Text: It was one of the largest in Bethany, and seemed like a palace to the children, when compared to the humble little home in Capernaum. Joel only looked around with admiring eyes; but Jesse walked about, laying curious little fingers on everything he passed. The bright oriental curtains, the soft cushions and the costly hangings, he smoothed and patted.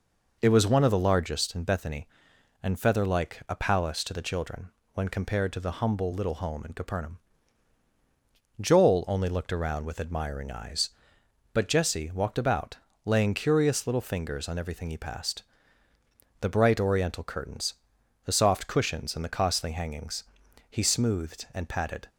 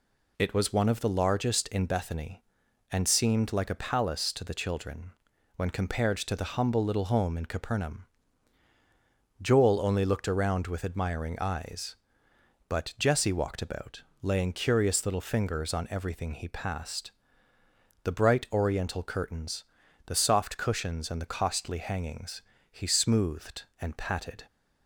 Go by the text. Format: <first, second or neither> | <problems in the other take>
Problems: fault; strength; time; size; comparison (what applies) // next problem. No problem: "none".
second | says "feather" for "seemed"; at 2.7 s